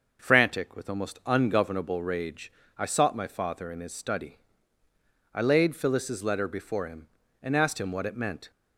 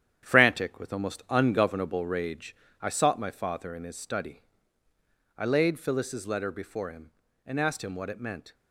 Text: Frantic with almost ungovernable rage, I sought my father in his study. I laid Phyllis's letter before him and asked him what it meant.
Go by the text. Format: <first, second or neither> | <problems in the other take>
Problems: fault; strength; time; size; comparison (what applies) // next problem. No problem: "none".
first | gets quieter; noticeable; throughout; 6 dB // starts louder than the rest; strong; until 1.3 s; 9.5 dB; noticeable in the first